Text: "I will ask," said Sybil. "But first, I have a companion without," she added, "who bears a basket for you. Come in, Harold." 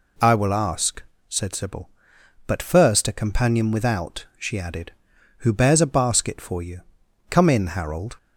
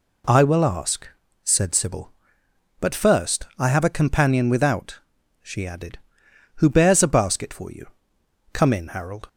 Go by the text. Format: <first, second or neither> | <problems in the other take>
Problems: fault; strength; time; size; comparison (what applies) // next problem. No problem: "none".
second | skips "I have"; at 3.0 s